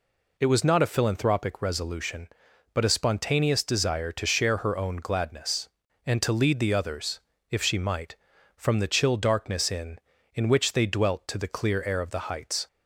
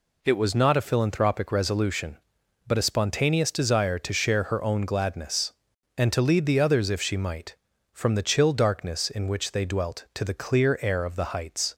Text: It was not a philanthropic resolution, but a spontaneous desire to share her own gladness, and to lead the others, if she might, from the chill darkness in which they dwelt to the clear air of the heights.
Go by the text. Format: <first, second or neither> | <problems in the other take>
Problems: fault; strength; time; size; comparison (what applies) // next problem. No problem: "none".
second | says "in" twice; at 10.3 s